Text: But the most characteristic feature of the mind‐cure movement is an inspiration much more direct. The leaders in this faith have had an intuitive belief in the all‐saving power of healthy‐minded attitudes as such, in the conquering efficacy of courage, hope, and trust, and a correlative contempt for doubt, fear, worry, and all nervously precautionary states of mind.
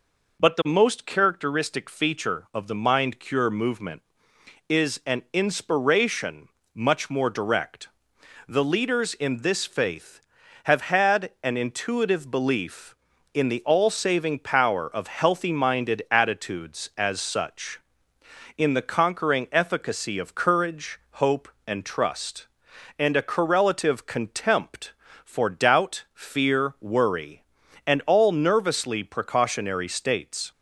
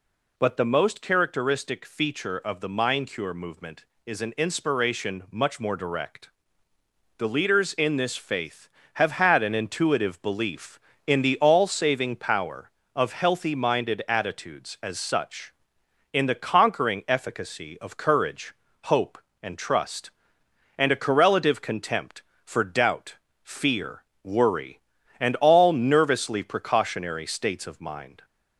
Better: second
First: pauses between "inspiration" and "much"; slight; at 6.4 s; 0.26 s long // stops before "of mind"; at 30.5 s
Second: none

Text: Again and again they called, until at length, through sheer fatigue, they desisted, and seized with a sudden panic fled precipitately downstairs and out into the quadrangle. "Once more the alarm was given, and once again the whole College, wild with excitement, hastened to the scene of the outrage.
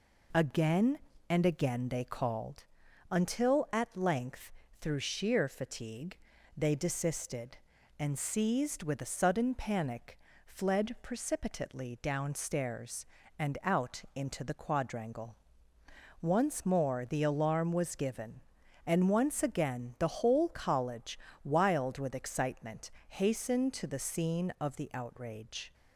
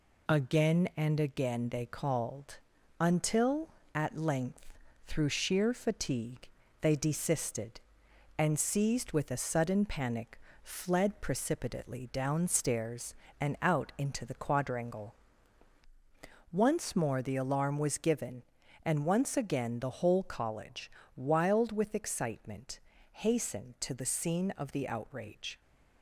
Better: neither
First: pauses between "panic" and "fled"; slight; at 10.1 s; 0.28 s long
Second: pauses between "panic" and "fled"; slight; at 10.4 s; 0.24 s long

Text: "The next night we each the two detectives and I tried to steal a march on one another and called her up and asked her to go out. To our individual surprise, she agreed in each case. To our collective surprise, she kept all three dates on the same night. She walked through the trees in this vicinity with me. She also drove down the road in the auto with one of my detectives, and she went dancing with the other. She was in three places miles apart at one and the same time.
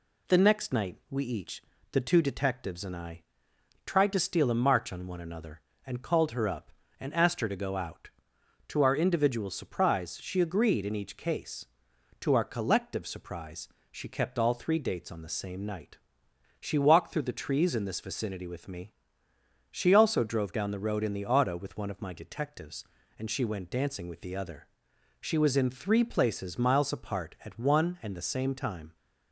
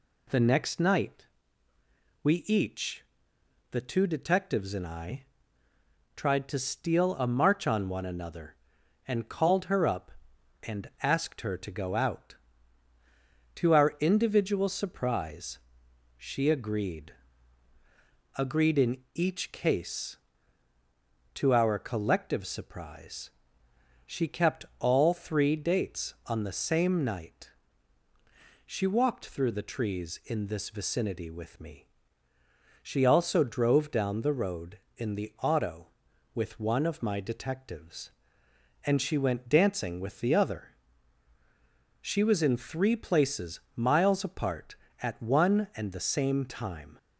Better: first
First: pauses between "each" and "the"; slight; at 1.6 s; 0.30 s long // pauses between "I" and "tried"; noticeable; at 3.2 s; 0.64 s long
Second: pauses between "night" and "we"; noticeable; at 1.2 s; 0.96 s long // pauses between "each" and "the"; noticeable; at 3.0 s; 0.68 s long // pauses between "I" and "tried"; noticeable; at 5.2 s; 0.92 s long // says "agreed" twice; at 18.3 s // pauses between "in" and "each"; slight; at 18.9 s; 0.16 s long

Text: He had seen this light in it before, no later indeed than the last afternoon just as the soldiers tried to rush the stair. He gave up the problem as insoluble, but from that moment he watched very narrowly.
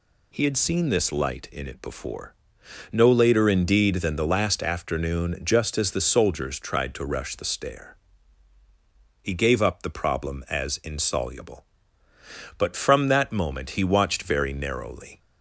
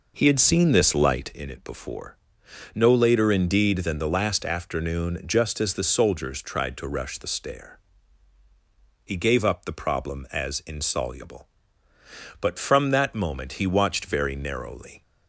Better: first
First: none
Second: starts louder than the rest; noticeable; until 1.4 s; 5 dB

